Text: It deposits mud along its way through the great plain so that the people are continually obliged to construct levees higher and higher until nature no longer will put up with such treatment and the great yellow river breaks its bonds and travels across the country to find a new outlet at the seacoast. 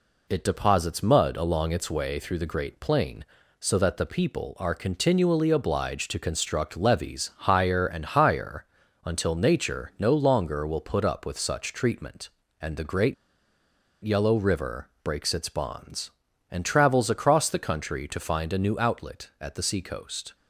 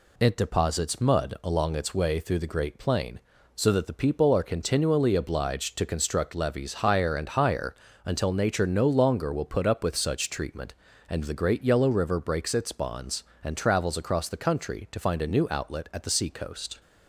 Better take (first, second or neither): second